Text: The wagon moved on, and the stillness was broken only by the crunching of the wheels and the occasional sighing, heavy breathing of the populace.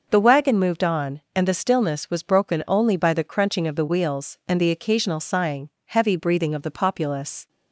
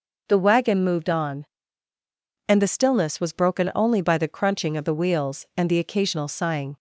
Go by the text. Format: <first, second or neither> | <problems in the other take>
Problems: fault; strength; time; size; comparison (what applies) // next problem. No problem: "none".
first | stops before "heavy breathing of the populace"; at 6.7 s